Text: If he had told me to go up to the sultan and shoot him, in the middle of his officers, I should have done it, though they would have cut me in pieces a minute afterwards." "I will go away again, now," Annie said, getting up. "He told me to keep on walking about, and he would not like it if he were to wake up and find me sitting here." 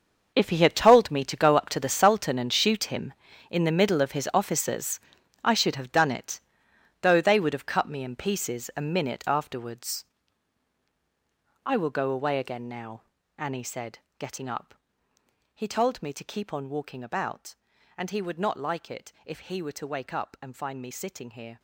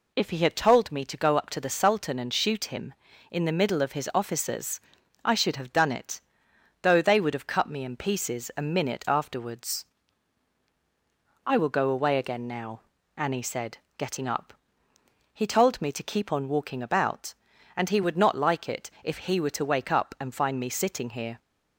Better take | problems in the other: second | gets quieter; strong; throughout; 14 dB

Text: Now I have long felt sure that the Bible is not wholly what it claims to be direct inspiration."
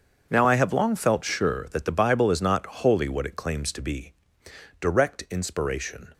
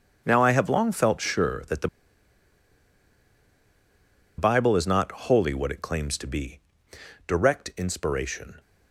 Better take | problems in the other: first | starts louder than the rest; until 1.2 s; 7 dB; also in the first // pauses between "the" and "Bible"; strong; at 1.8 s; 2.4 s long // pauses between "be" and "direct"; noticeable; at 6.5 s; 0.68 s long; noticeable in the first

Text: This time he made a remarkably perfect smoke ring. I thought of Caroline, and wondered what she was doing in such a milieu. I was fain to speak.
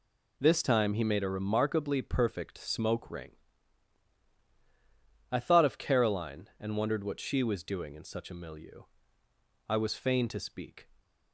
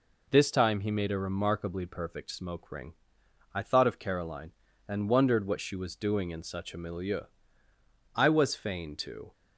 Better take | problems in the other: first | stops before "speak"; at 9.3 s

